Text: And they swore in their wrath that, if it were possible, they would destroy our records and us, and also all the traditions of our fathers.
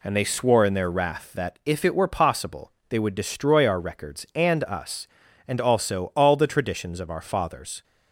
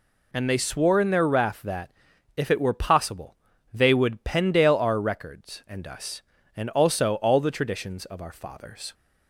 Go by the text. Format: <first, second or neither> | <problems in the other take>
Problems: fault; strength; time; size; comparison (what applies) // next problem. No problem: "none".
first | says "pendale" for "destroy"; at 4.2 s